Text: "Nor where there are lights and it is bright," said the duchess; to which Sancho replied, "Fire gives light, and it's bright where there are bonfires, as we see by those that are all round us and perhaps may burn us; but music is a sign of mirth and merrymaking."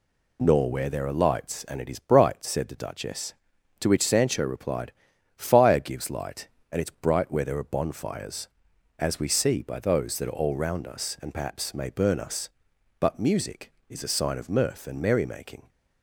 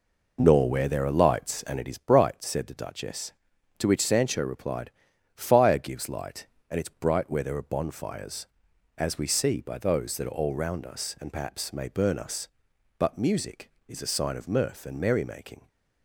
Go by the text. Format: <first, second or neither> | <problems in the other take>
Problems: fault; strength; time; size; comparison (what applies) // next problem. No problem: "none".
first | starts louder than the rest; noticeable; until 2.0 s; 4.5 dB